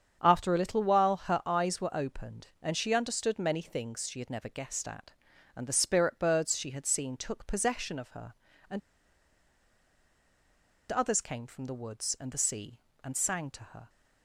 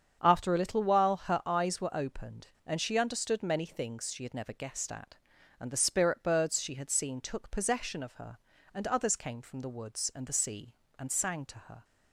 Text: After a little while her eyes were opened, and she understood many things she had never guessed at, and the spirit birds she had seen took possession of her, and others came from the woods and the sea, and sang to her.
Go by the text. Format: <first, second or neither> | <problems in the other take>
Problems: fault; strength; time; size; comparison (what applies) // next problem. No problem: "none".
second | starts louder than the rest; strong; until 1.2 s; 7.5 dB; strong in the second // pauses between "and" and "others"; strong; at 8.8 s; 2.1 s long